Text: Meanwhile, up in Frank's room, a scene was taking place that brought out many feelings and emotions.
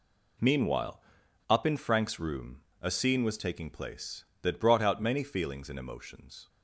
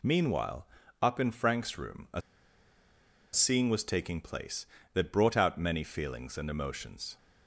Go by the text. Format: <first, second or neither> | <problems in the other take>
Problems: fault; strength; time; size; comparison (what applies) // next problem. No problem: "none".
first | pauses between "a" and "scene"; at 2.2 s; 1.1 s long